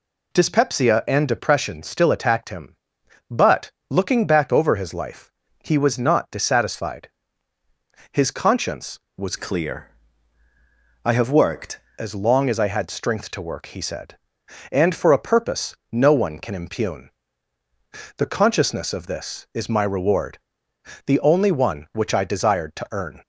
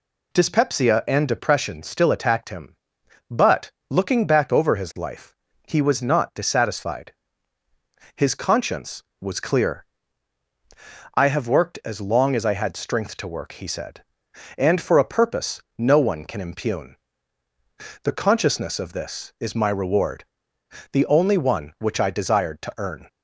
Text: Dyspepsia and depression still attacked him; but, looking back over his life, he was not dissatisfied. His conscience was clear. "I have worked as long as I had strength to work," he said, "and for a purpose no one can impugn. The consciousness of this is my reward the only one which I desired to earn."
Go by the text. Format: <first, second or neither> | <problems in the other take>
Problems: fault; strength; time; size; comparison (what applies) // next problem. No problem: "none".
second | changes voice from "clear" to "worked"; from 9.3 to 11.8 s; 2.5 s long // pauses between "purpose" and "no"; slight; at 15.7 s; 0.16 s long; slight in the second // pauses between "reward" and "the"; noticeable; at 20.3 s; 0.68 s long; noticeable in the second